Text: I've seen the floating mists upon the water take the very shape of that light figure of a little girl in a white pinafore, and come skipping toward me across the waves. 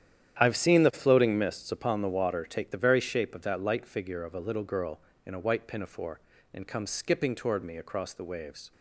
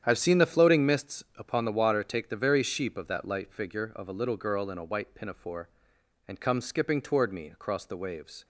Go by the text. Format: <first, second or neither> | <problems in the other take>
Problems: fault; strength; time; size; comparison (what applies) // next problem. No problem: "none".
first | starts louder than the rest; strong; until 1.0 s; 9.5 dB; strong in the first // says "sheep" for "shape"; at 2.6 s